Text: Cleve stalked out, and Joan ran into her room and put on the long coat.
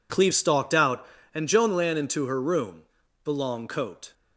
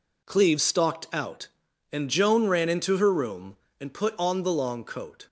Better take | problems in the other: second | skips "and put on"; at 3.0 s

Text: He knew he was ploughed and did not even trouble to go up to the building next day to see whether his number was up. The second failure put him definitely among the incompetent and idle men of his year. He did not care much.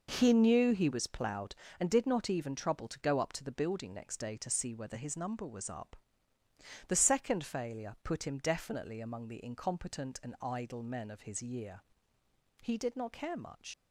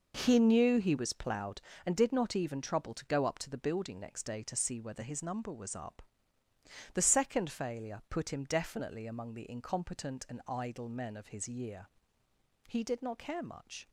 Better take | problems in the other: second | leaves "much" unfinished; at 13.7 s; 95 ms

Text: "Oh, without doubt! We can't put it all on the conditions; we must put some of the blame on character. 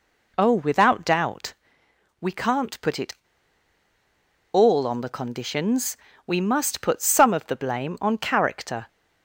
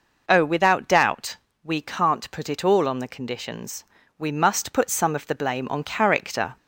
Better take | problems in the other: second | pauses between "it" and "all"; strong; at 3.1 s; 1.3 s long

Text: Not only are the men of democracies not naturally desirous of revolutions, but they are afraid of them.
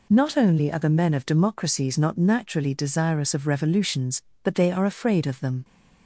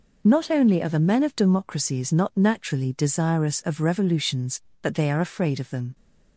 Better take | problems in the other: neither | none

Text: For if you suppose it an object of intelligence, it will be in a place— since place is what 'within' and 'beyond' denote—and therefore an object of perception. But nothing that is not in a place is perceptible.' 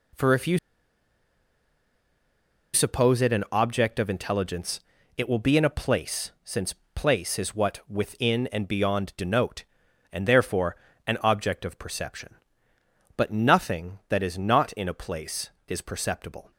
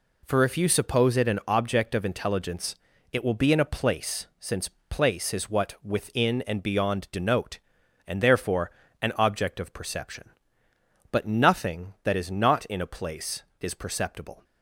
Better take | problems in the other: second | pauses between "you" and "suppose"; strong; at 0.5 s; 2.1 s long // pauses between "since" and "place"; slight; at 6.7 s; 0.18 s long; slight in the second // pauses between "therefore" and "an"; slight; at 10.7 s; 0.32 s long; slight in the second

